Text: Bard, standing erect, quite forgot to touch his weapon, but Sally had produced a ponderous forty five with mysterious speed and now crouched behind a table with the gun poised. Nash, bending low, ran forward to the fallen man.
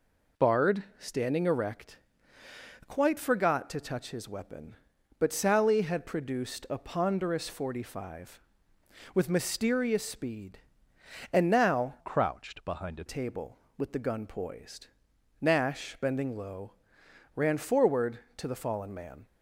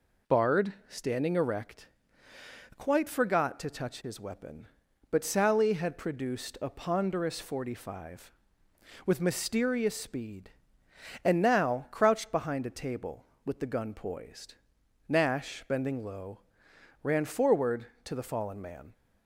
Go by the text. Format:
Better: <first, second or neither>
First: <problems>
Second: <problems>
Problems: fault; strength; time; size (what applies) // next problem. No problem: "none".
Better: second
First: changes voice from "crouched" to "a"; from 11.9 to 13.0 s; 1.1 s long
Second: none